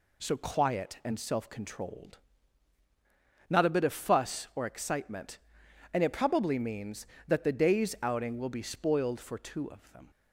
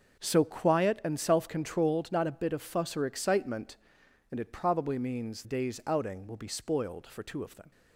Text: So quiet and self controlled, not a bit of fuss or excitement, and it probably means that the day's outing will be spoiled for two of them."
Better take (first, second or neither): first